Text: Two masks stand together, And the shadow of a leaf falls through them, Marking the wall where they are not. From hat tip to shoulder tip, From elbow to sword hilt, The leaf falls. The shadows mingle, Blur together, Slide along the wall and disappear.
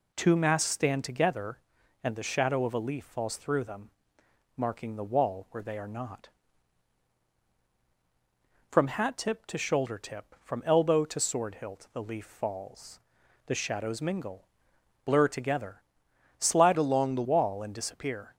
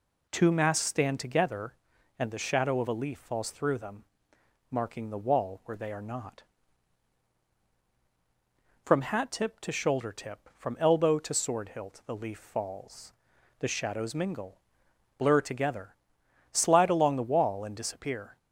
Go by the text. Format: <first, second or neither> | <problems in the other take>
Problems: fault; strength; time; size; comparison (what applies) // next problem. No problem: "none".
second | changes voice from "along" to "the"; from 16.7 to 17.2 s; 0.5 s long